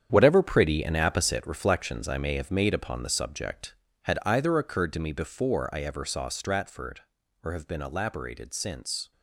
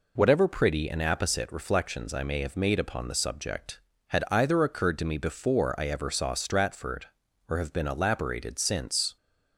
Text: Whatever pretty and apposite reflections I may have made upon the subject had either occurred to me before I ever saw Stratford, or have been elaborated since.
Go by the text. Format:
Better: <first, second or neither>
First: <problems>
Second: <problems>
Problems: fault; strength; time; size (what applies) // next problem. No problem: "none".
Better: second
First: gets quieter; strong; throughout; 10 dB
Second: none